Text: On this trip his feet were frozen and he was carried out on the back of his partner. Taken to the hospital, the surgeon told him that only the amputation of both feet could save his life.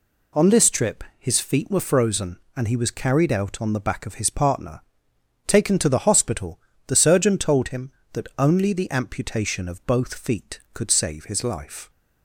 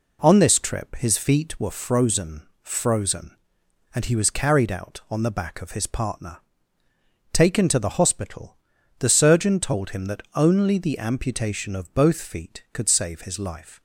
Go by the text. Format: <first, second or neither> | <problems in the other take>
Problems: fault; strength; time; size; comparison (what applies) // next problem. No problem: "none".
first | says "frozen" twice; at 2.6 s